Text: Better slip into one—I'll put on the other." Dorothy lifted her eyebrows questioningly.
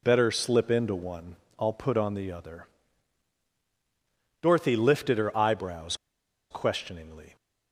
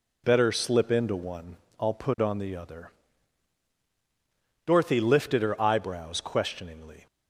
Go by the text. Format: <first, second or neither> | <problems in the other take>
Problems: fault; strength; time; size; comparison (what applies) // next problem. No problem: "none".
second | pauses between "eyebrows" and "questioningly"; noticeable; at 5.9 s; 0.54 s long